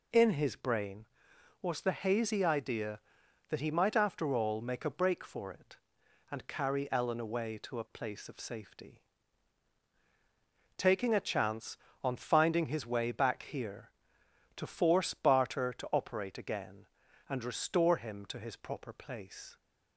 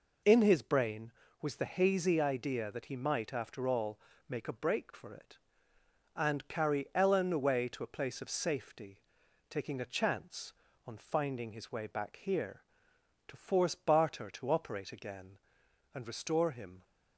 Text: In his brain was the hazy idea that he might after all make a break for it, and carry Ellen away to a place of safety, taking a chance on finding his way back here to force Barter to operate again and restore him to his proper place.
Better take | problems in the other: first | pauses between "all" and "make"; slight; at 3.9 s; 0.30 s long // stops before "to his proper place"; at 16.8 s

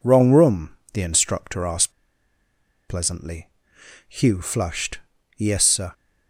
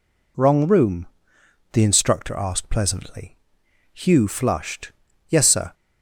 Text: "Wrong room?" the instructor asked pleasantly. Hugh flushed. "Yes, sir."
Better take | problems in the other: second | pauses between "asked" and "pleasantly"; noticeable; at 1.9 s; 0.96 s long

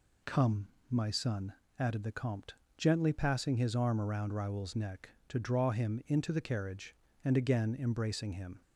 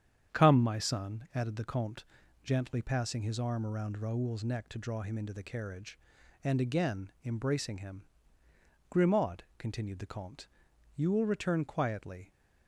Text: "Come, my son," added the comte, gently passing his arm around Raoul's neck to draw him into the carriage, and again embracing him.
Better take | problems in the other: first | starts louder than the rest; strong; until 1.4 s; 8.5 dB // goes on to say "Grimaud continued the comte you will return quietly"; strong; from 8.8 s on; 3.4 s long

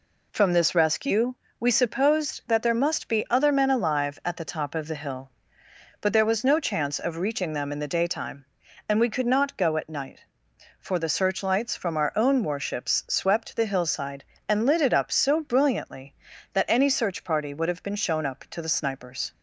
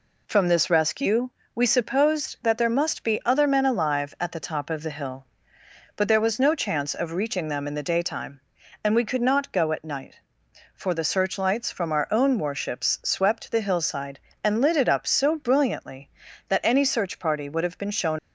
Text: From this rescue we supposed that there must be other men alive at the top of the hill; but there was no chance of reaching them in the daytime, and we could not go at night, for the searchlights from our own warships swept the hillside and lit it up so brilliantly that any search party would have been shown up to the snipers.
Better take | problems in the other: first | pauses between "rescue" and "we"; slight; at 1.3 s; 0.24 s long; slight in the first // stops before "up to the snipers"; at 18.1 s

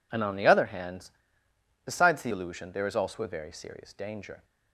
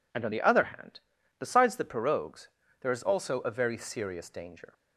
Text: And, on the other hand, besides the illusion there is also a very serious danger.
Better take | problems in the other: first | says "pirogues" for "illusion"; at 1.8 s

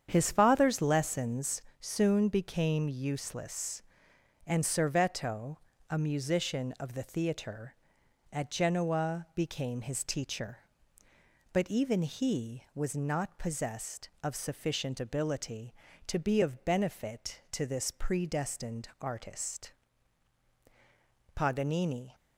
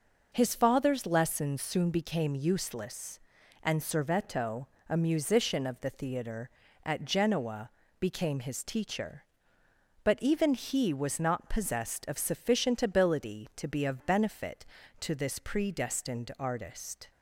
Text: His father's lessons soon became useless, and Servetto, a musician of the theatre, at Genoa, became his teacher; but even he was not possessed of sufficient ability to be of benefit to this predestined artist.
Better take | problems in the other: second | starts louder than the rest; strong; until 1.1 s; 8 dB // pauses between "lessons" and "soon"; slight; at 1.6 s; 0.18 s long // goes on to say "Paganini"; noticeable; from 21.3 s on; 0.80 s long

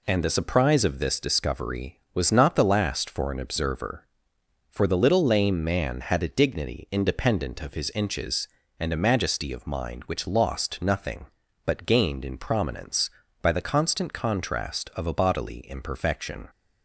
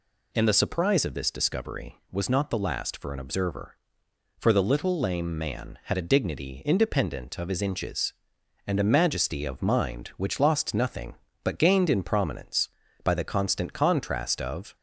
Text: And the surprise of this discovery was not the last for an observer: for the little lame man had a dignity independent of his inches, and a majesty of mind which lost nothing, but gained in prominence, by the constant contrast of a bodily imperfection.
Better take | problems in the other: first | stops before "a bodily imperfection"; at 14.7 s

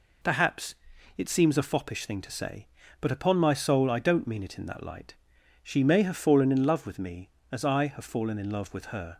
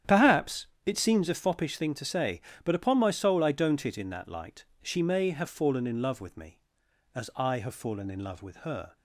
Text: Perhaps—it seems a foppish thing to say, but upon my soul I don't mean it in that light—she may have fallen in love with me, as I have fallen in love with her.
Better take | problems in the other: first | starts louder than the rest; strong; until 1.2 s; 9.5 dB // skips "mean"; at 3.8 s

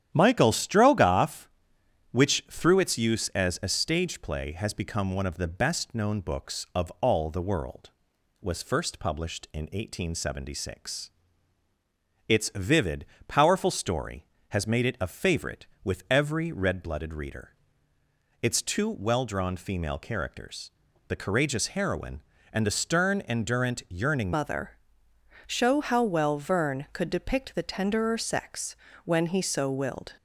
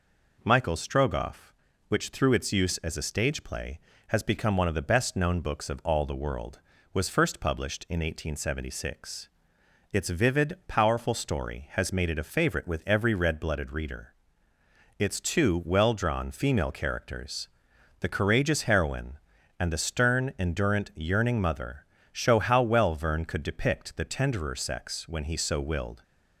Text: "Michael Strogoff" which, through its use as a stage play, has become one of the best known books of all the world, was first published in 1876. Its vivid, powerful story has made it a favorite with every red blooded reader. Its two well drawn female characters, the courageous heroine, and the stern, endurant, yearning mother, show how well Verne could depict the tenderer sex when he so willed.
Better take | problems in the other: second | starts louder than the rest; strong; until 1.1 s; 10.5 dB // changes voice at "mother"; from 24.3 s on; 5.8 s long // pauses between "sex" and "when"; slight; at 28.7 s; 0.28 s long

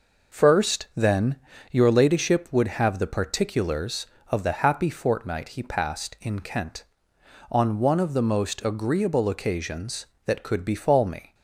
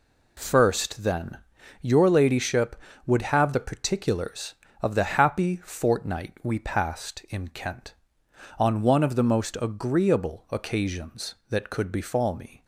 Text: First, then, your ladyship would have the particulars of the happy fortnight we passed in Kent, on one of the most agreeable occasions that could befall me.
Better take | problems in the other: second | says "he" for "we"; at 5.4 s

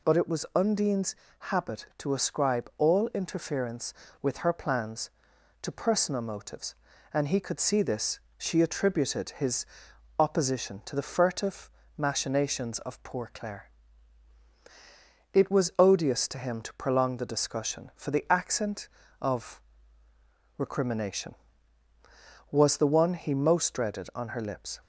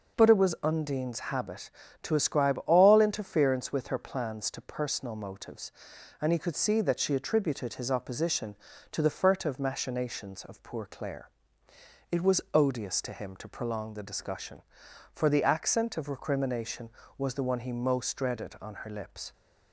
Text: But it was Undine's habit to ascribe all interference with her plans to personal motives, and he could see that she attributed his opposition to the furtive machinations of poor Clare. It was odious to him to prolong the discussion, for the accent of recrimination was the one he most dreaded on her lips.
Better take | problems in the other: second | pauses between "Undine's" and "habit"; slight; at 1.1 s; 0.22 s long // says "this" for "that"; at 7.8 s // pauses between "his" and "opposition"; noticeable; at 9.6 s; 0.54 s long // pauses between "furtive" and "machinations"; slight; at 11.7 s; 0.26 s long // pauses between "of" and "recrimination"; noticeable; at 19.6 s; 0.98 s long

